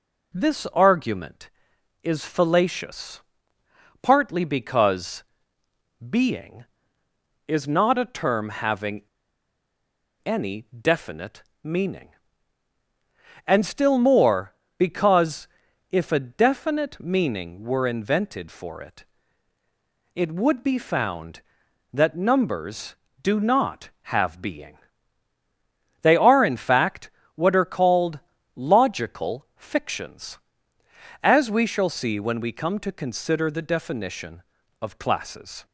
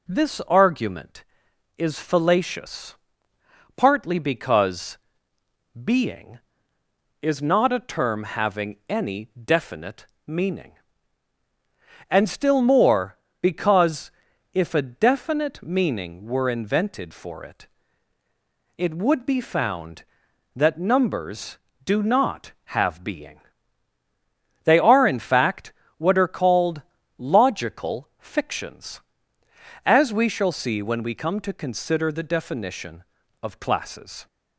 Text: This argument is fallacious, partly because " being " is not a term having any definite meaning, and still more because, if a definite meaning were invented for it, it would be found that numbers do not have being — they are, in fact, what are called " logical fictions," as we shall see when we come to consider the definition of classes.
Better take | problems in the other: second | pauses between "having" and "any"; at 9.0 s; 1.2 s long // pauses between "definite" and "meaning"; slight; at 11.4 s; 0.18 s long; slight in the second

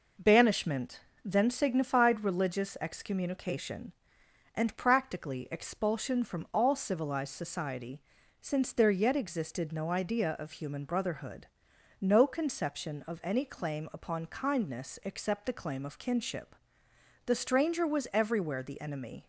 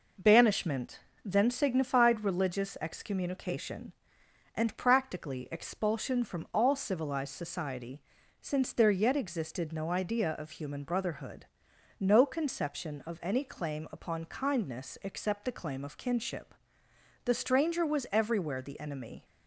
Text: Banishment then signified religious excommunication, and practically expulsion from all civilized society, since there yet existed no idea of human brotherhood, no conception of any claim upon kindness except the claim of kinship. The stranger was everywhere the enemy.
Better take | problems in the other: neither | pauses between "Banishment" and "then"; slight; the same in both

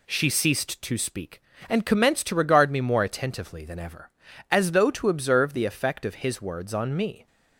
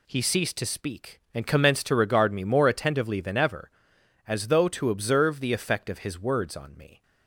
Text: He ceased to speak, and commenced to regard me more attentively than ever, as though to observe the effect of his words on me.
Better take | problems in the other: second | says "She" for "He"; at 0.0 s

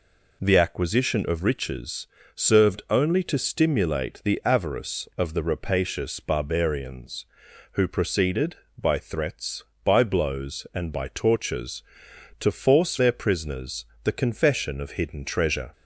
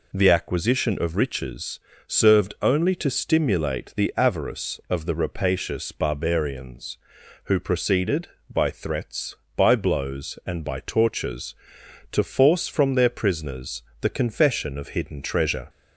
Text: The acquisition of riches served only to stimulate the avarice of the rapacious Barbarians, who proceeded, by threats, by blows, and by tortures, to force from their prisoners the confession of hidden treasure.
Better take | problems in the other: second | pauses between "riches" and "served"; slight; at 2.0 s; 0.28 s long; slight in the second // skips "from"; at 12.9 s // pauses between "prisoners" and "the"; slight; at 13.8 s; 0.18 s long; slight in the second

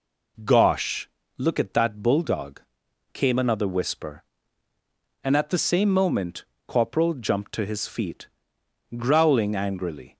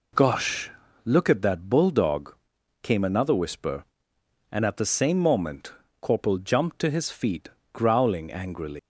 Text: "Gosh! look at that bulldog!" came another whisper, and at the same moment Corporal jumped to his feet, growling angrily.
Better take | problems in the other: first | pauses between "moment" and "Corporal"; slight; at 5.7 s; 0.28 s long; slight in the first // leaves "angrily" unfinished; at 8.7 s; 145 ms

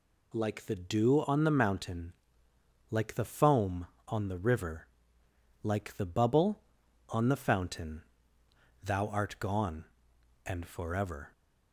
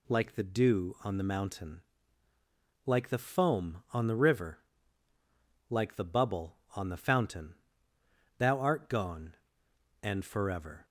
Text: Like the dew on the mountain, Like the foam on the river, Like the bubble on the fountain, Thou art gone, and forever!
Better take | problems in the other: neither | none

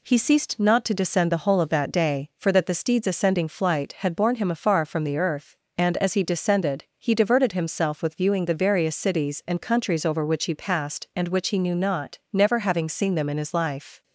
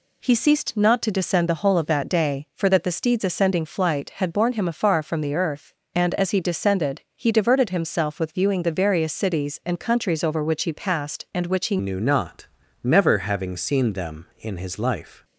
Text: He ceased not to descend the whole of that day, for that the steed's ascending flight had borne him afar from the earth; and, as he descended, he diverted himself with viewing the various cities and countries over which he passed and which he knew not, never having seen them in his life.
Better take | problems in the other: first | changes voice at "knew"; from 11.7 s on; 3.5 s long

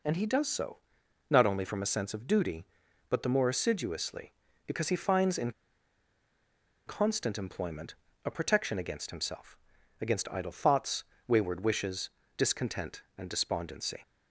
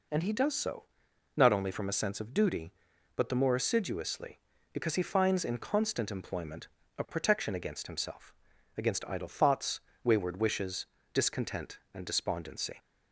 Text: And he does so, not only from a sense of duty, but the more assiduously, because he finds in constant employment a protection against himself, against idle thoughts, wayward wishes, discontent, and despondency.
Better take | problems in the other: second | pauses between "in" and "constant"; strong; at 5.5 s; 1.3 s long // pauses between "employment" and "a"; slight; at 7.9 s; 0.32 s long; slight in the second

